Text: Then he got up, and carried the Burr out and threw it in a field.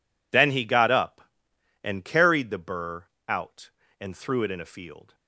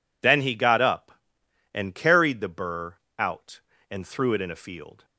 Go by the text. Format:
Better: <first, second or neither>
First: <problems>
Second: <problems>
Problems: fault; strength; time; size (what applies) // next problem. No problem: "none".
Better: second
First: gets quieter; strong; throughout; 19 dB // pauses between "Burr" and "out"; slight; at 3.0 s; 0.24 s long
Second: pauses between "Burr" and "out"; slight; at 2.9 s; 0.24 s long